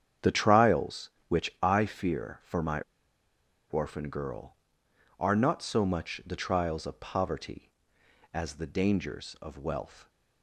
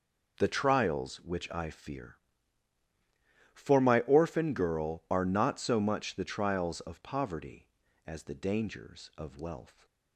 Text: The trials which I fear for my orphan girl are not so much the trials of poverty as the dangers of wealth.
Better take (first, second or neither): second